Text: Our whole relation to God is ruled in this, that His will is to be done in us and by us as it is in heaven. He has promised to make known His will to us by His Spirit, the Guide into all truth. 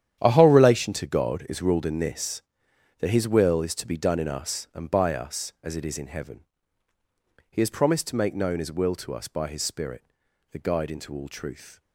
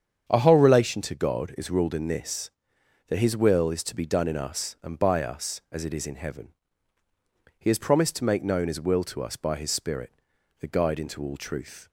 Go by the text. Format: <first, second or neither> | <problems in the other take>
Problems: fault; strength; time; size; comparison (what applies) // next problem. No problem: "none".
second | gets quieter; strong; throughout; 13.5 dB // starts louder than the rest; strong; until 1.2 s; 10 dB; strong in the second